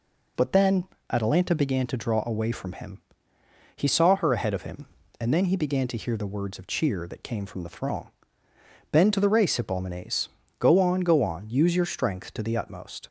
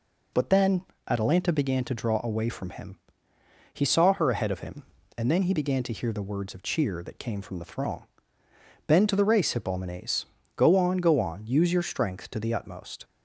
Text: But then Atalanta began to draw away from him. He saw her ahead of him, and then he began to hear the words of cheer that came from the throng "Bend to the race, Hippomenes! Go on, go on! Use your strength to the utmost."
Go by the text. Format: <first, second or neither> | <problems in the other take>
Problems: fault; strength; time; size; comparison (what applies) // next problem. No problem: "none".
neither | pauses between "then" and "Atalanta"; slight; the same in both // pauses between "throng" and "Bend"; noticeable; the same in both